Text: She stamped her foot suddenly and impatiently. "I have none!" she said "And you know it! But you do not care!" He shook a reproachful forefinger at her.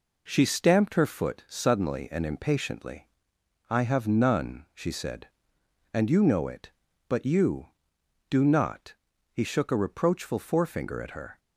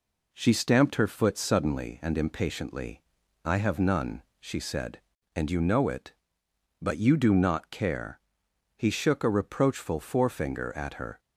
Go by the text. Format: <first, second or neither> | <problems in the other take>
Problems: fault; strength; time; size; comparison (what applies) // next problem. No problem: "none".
second | skips "care"; at 9.1 s